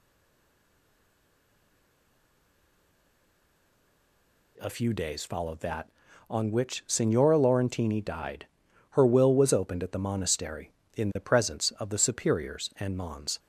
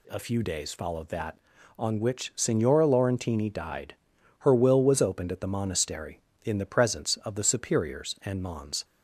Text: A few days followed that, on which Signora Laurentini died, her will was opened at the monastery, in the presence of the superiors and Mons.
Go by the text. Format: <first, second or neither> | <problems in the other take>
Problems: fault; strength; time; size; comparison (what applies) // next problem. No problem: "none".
second | stays silent before the first word; strong; until 4.5 s; 4.5 s long